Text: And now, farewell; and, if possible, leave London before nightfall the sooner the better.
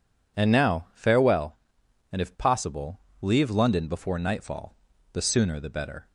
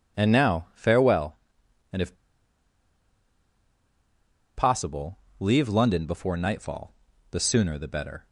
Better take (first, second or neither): first